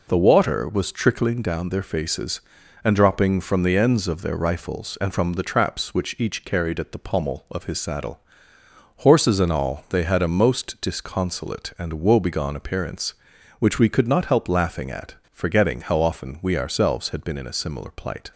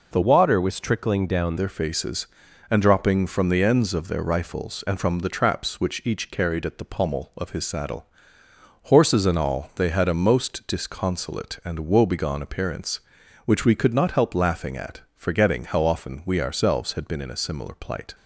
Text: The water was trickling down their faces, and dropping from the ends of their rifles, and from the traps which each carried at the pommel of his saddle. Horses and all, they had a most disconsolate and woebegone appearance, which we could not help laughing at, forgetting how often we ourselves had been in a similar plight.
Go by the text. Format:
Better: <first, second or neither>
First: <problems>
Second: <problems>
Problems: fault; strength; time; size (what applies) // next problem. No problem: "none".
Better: first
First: none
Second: changes voice from "water" to "down"; from 0.2 to 1.5 s; 1.3 s long